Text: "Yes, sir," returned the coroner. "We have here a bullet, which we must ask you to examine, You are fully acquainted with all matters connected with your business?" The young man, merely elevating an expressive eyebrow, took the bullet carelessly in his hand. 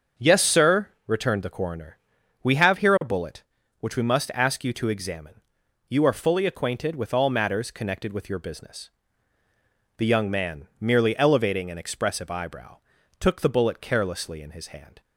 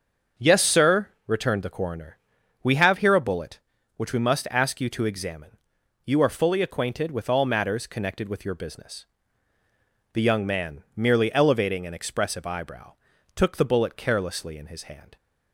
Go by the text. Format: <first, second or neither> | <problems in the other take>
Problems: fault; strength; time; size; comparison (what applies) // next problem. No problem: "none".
neither | starts louder than the rest; the same in both